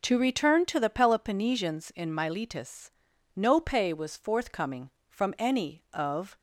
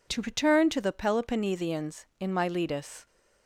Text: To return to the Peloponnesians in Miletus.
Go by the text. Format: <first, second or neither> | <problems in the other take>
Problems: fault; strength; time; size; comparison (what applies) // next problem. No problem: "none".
second | goes on to say "No pay was forthcoming from any of"; strong; from 3.3 s on; 3.0 s long